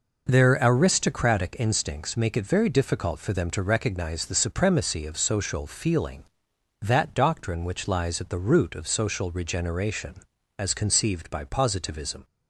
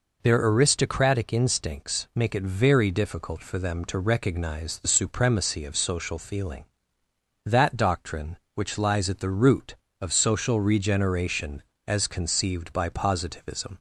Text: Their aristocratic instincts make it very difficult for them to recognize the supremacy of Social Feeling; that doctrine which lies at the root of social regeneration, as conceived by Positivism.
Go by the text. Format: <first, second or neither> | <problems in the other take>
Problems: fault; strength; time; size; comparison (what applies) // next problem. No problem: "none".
neither | none